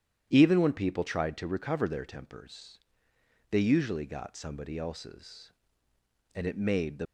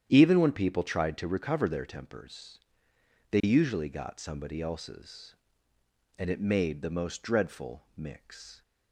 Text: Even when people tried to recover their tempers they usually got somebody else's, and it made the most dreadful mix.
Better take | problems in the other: second | starts louder than the rest; strong; until 1.3 s; 10 dB; strong in the second // pauses between "tempers" and "they"; noticeable; at 2.7 s; 0.72 s long; noticeable in the second // stops before "most dreadful mix"; at 7.0 s

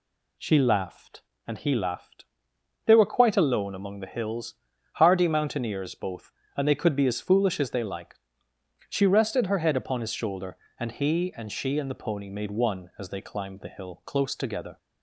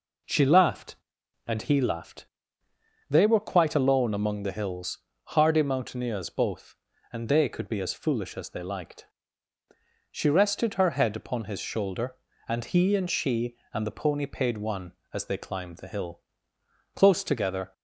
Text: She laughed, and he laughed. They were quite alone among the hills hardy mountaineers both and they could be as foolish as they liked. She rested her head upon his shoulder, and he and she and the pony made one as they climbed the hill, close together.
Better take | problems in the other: first | pauses between "hills" and "hardy"; slight; at 4.9 s; 0.30 s long; also in the first // says "paid" for "made"; at 14.2 s

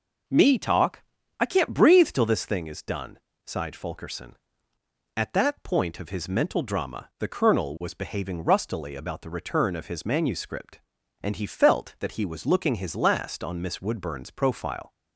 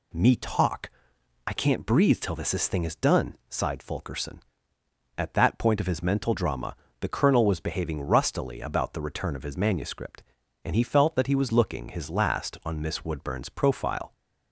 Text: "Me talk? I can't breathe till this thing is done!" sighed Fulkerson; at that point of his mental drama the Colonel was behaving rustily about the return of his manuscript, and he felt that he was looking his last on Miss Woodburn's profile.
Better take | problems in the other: first | says "this" twice; at 2.5 s // pauses between "drama" and "the"; slight; at 6.7 s; 0.24 s long

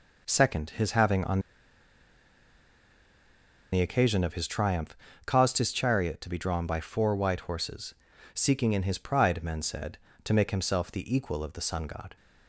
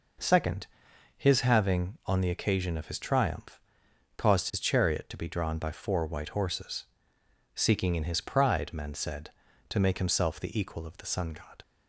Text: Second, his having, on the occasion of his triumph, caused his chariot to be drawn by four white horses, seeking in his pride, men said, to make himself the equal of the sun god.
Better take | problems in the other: second | pauses between "on" and "the"; strong; at 1.3 s; 2.3 s long

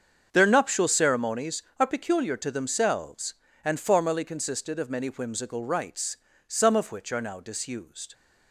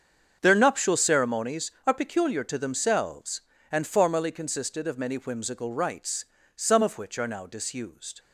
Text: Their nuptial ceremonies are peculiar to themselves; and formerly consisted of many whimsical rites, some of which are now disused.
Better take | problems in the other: neither | starts louder than the rest; strong; the same in both

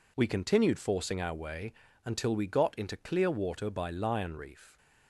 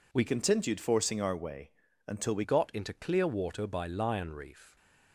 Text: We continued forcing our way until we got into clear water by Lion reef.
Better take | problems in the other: first | changes voice from "continued" to "we"; from 0.2 to 2.4 s; 2.2 s long // pauses between "way" and "until"; slight; at 1.7 s; 0.34 s long; slight in the first

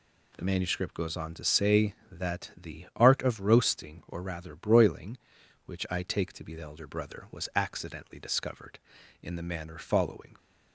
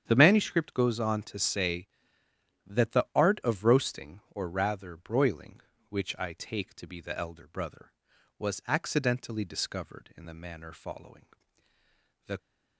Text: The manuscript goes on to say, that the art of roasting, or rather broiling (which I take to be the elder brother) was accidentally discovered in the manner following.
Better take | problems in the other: first | starts louder than the rest; strong; until 1.0 s; 8.5 dB // goes on to say "The"; slight; from 12.2 s on; 0.10 s long

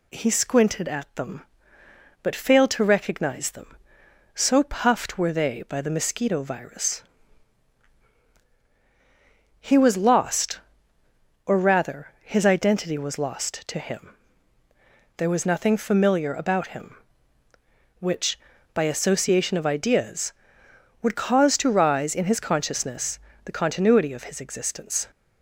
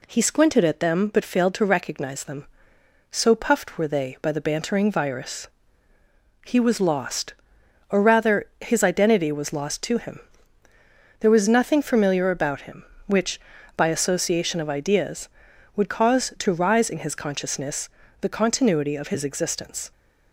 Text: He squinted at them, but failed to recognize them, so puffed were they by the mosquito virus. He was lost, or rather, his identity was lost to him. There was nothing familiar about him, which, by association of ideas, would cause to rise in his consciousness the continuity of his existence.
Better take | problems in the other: first | says "bantering" for "mosquito"; at 4.4 s // pauses between "consciousness" and "the"; slight; at 17.8 s; 0.34 s long; slight in the first

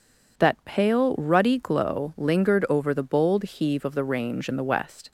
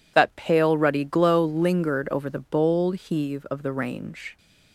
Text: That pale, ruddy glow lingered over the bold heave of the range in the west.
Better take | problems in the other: first | stops before "in the west"; at 4.3 s

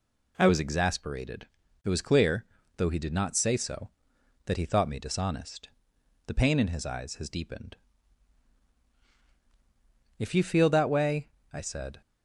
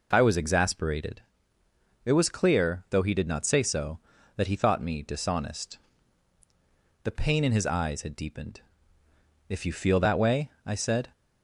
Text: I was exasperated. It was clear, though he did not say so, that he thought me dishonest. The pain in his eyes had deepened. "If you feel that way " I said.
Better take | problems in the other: second | says "has" for "had"; at 7.1 s

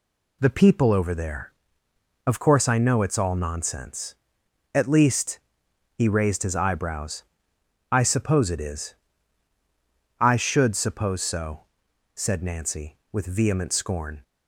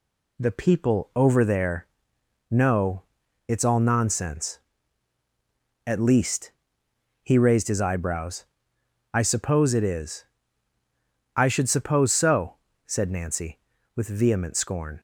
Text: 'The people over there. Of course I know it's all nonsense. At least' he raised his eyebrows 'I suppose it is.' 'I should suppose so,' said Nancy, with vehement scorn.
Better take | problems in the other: first | skips "Of course I"; at 2.1 s // pauses between "know" and "it's"; noticeable; at 3.0 s; 0.46 s long // pauses between "least" and "he"; noticeable; at 6.4 s; 0.72 s long; noticeable in the first // pauses between "eyebrows" and "I"; noticeable; at 8.4 s; 0.70 s long; noticeable in the first

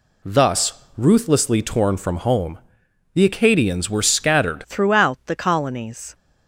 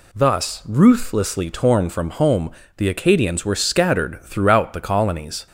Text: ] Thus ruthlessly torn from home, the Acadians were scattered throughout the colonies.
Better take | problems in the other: second | changes voice at "throughout"; from 4.6 s on; 1.5 s long

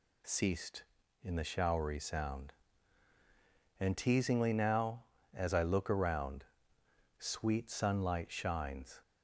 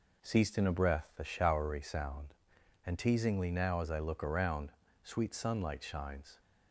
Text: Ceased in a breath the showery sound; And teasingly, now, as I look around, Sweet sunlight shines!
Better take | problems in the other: second | skips "a breath"; at 1.3 s

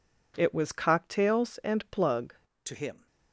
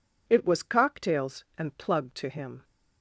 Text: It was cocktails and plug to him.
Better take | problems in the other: second | changes voice at "to"; from 2.6 s on; 0.4 s long

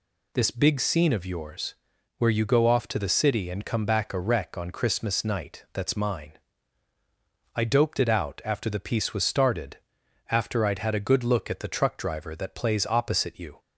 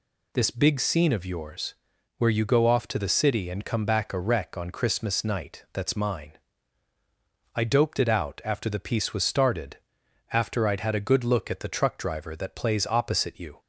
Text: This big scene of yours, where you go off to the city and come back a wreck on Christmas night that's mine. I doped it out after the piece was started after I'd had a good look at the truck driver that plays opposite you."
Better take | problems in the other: neither | pauses between "started" and "after"; noticeable; the same in both

